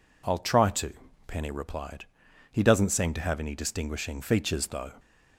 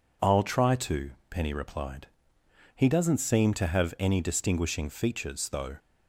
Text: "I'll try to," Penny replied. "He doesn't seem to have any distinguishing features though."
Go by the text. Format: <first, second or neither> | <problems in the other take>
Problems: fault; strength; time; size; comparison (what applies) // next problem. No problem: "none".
neither | none